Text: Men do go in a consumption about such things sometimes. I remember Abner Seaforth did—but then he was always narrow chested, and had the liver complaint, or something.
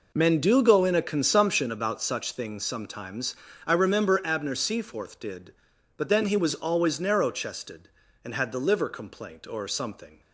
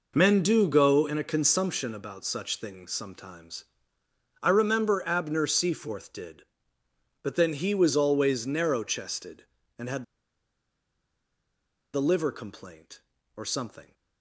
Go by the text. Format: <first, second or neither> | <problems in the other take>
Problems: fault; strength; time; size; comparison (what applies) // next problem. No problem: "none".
first | pauses between "had" and "the"; strong; at 10.0 s; 1.8 s long